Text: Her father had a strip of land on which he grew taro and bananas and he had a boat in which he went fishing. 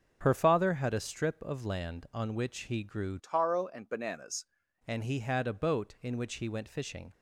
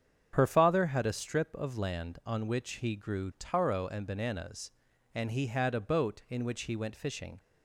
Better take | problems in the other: second | starts louder than the rest; until 1.2 s; 6.5 dB; strong in the second // changes voice from "taro" to "bananas"; from 3.1 to 4.4 s; 1.3 s long

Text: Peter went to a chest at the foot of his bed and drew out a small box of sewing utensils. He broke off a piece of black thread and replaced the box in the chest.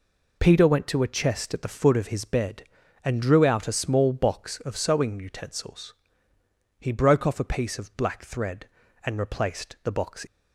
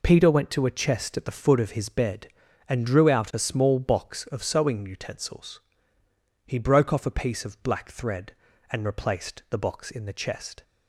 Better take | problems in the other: second | stops before "in the chest"; at 10.2 s

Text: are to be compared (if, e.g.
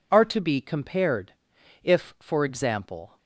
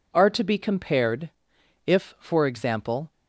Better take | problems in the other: neither | none

